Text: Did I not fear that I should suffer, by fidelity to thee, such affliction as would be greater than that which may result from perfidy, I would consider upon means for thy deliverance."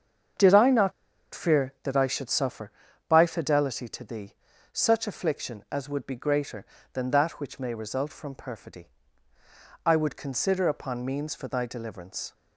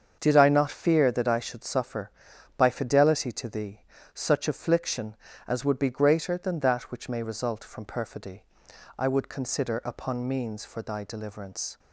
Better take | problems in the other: second | starts louder than the rest; until 1.9 s; 7 dB; also in the second // pauses between "not" and "fear"; at 0.9 s; 0.41 s long

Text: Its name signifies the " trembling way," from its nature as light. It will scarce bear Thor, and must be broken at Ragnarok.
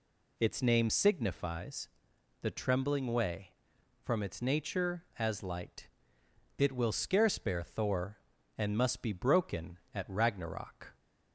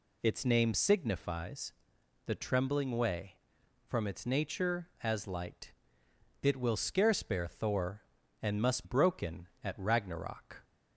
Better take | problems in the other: first | pauses between "signifies" and "the"; noticeable; at 1.7 s; 0.54 s long; noticeable in the first // skips "be"; at 8.8 s

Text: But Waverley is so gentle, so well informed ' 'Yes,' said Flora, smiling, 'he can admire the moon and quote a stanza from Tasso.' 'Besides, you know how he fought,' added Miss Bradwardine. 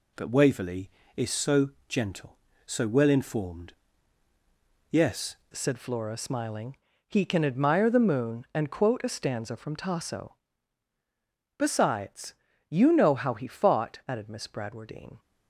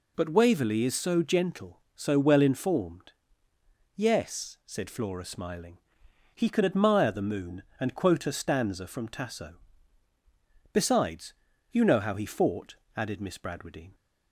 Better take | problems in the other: second | pauses between "so" and "gentle"; slight; at 1.6 s; 0.18 s long // changes voice at "said"; from 5.5 s on; 9.6 s long

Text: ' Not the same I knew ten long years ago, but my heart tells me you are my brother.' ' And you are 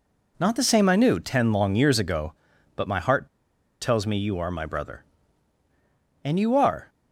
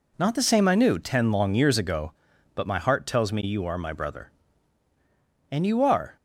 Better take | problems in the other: second | pauses between "heart" and "tells"; noticeable; at 3.2 s; 0.55 s long

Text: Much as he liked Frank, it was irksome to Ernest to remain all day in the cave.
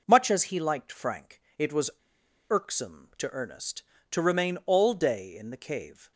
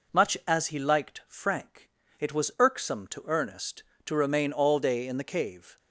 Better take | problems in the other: second | pauses between "was" and "irksome"; noticeable; at 1.8 s; 0.60 s long

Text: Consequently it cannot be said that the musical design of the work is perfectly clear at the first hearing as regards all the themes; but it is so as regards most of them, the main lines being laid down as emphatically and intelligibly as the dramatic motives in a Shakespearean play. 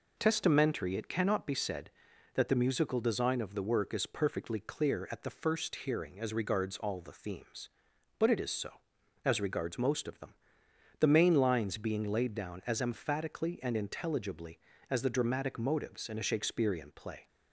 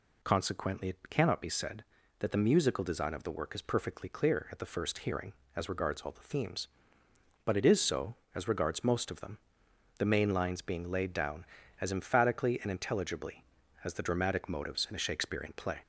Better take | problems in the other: second | says "Testamentary" for "Consequently"; at 0.1 s

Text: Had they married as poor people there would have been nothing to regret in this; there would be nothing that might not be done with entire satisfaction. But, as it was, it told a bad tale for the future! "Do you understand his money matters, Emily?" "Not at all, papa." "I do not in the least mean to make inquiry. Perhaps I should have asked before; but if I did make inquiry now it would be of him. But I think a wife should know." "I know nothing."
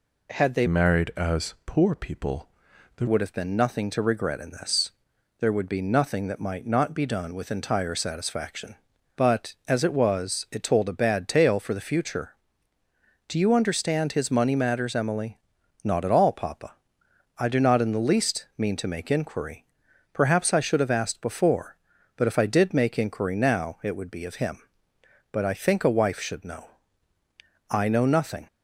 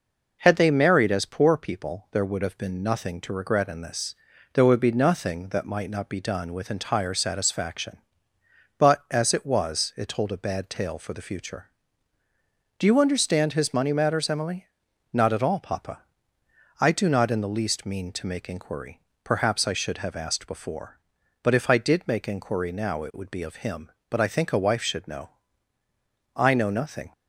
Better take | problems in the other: second | changes voice from "married" to "there"; from 0.6 to 3.0 s; 2.4 s long // pauses between "people" and "there"; noticeable; at 2.4 s; 0.48 s long

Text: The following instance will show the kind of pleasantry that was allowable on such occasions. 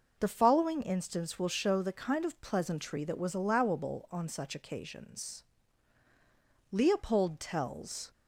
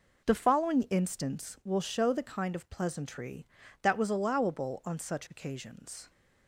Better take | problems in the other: second | goes on to say "Leopold tells"; from 6.7 s on; 1.4 s long

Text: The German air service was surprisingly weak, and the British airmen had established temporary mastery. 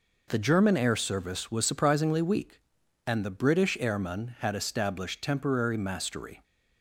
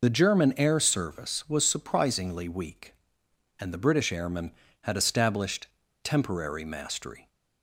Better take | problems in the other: first | loses the start of "The"; at 0.0 s; 40 ms // pauses between "established" and "temporary"; slight; at 5.6 s; 0.34 s long

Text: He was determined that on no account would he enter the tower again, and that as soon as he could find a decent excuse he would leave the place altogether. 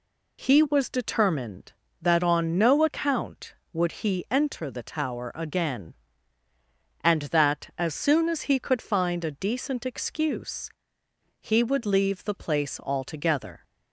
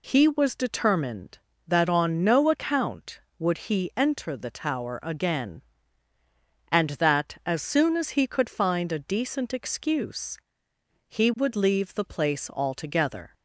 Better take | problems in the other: neither | pauses between "excuse" and "he"; noticeable; the same in both

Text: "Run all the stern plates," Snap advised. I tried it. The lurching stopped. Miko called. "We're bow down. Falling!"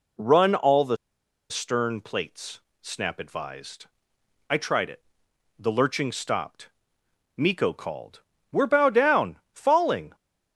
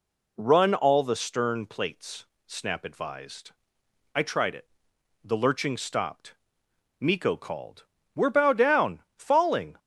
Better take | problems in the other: second | pauses between "the" and "stern"; noticeable; at 0.9 s; 0.54 s long

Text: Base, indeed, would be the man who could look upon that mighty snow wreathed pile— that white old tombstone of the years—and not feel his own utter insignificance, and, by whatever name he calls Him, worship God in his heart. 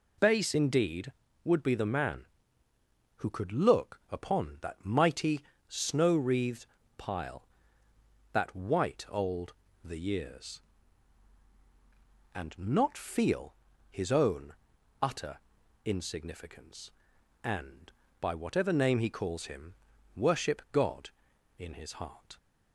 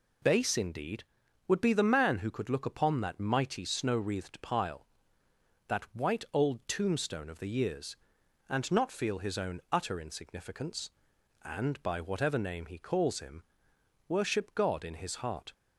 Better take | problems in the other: second | pauses between "mighty" and "snow"; slight; at 5.4 s; 0.28 s long // pauses between "wreathed" and "pile"; slight; at 6.6 s; 0.32 s long // skips "tombstone of"; at 9.6 s // pauses between "feel" and "his"; slight; at 13.5 s; 0.33 s long // pauses between "own" and "utter"; noticeable; at 14.5 s; 0.48 s long // pauses between "utter" and "insignificance"; noticeable; at 15.3 s; 0.46 s long

